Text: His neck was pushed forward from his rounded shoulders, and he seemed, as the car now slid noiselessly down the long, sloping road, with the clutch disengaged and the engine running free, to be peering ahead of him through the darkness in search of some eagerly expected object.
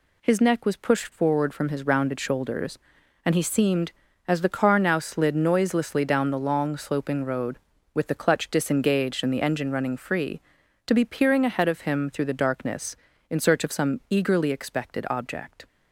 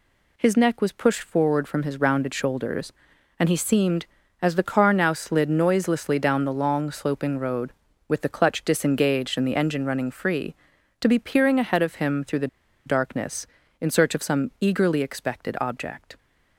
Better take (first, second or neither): first